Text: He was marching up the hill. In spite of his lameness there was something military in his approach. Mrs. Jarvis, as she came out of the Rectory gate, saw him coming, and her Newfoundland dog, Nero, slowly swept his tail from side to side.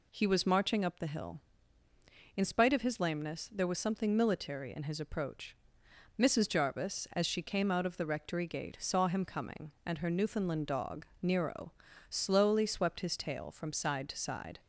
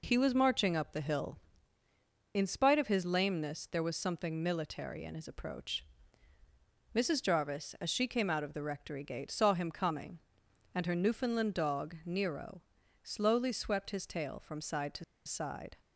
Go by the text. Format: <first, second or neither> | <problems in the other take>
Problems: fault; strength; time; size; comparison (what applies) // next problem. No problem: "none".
first | pauses between "to" and "side"; slight; at 15.0 s; 0.23 s long